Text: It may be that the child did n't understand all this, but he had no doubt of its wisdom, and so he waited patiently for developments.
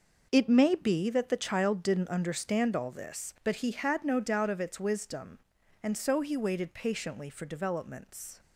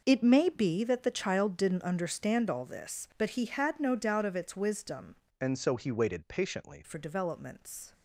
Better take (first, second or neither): first